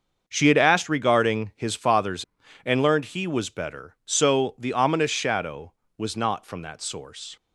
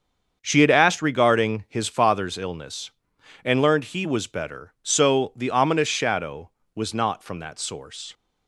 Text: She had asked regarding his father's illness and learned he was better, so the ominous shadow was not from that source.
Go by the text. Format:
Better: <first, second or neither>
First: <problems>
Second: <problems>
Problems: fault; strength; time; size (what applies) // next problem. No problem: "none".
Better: second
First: starts louder than the rest; until 1.2 s; 6.5 dB // skips "illness"; at 2.4 s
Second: starts louder than the rest; until 1.4 s; 7 dB